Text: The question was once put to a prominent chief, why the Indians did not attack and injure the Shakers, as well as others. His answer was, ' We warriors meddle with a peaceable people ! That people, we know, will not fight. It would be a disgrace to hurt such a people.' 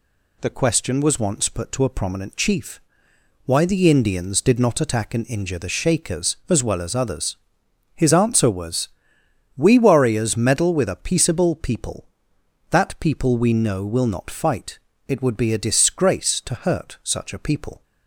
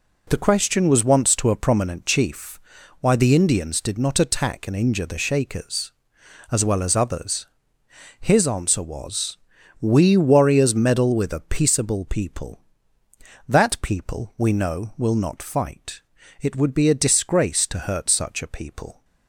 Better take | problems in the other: first | skips "put"; at 1.3 s

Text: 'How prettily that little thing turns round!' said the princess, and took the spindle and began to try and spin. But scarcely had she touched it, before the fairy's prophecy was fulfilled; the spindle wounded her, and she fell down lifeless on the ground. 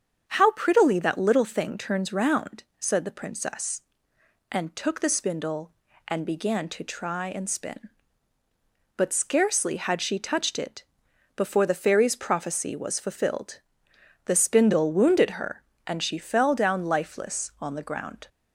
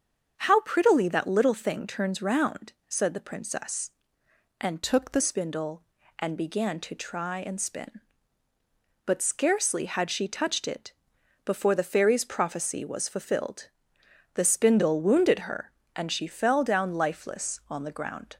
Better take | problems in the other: first | starts louder than the rest; until 1.3 s; 7 dB; strong in the first // changes voice from "took" to "the"; from 4.8 to 5.2 s; 0.4 s long

